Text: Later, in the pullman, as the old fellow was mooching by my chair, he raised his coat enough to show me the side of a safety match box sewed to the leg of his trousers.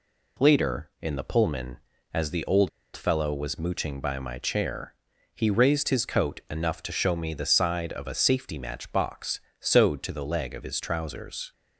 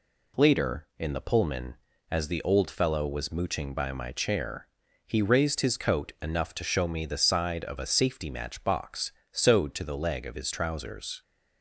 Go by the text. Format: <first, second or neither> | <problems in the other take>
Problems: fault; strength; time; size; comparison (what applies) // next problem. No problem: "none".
second | pauses between "old" and "fellow"; slight; at 2.6 s; 0.25 s long // pauses between "box" and "sewed"; slight; at 9.3 s; 0.20 s long; slight in the second